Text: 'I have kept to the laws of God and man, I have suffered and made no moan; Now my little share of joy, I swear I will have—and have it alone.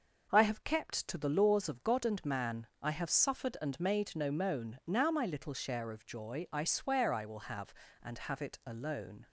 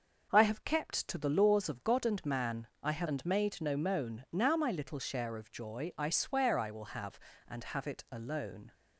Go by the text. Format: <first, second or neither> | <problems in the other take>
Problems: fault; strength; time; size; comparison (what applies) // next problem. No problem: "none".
first | starts louder than the rest; noticeable; until 1.3 s; 6 dB // skips "suffered"; at 3.0 s